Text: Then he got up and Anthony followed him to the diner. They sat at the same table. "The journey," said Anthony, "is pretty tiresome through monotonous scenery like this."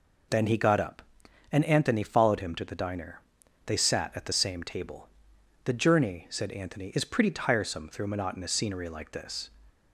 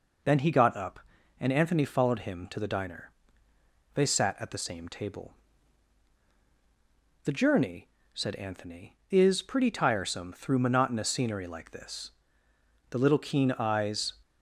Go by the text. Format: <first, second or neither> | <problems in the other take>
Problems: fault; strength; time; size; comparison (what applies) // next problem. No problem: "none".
first | goes on to say "The little keen eyes"; noticeable; from 12.8 s on; 1.2 s long